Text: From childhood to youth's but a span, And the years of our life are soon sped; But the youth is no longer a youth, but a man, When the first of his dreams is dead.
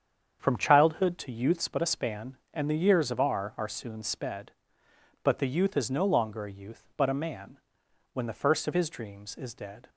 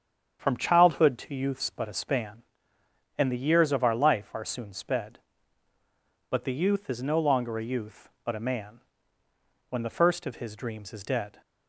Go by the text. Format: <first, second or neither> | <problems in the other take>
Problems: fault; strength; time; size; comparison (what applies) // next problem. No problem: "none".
second | starts louder than the rest; strong; until 1.4 s; 7.5 dB; strong in the second // skips "life"; at 3.5 s